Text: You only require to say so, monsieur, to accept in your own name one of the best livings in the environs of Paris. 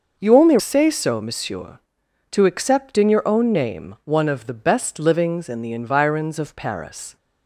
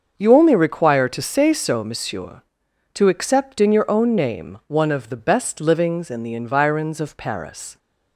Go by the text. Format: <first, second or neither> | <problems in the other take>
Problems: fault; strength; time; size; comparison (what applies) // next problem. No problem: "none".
second | starts louder than the rest; noticeable; until 1.2 s; 6 dB; also in the second // skips "require to"; at 0.5 s